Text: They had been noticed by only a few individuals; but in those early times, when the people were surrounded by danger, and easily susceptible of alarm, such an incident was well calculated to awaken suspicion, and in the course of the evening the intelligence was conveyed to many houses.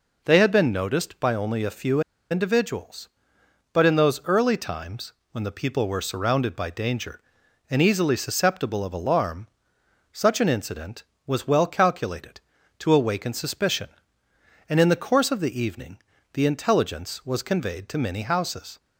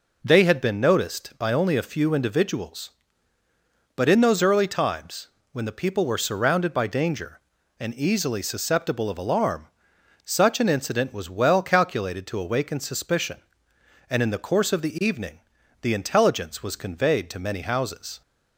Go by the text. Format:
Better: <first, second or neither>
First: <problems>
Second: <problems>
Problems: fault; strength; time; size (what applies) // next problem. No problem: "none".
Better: second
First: pauses between "few" and "individuals"; slight; at 2.0 s; 0.30 s long // pauses between "evening" and "the"; slight; at 16.0 s; 0.30 s long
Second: pauses between "evening" and "the"; at 15.4 s; 0.40 s long